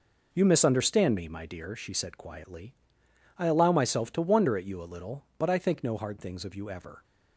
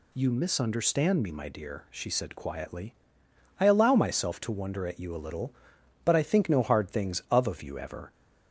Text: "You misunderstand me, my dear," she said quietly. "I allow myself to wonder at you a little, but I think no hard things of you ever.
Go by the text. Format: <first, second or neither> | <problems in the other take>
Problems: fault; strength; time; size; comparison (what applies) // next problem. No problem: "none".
first | says "of" twice; at 7.4 s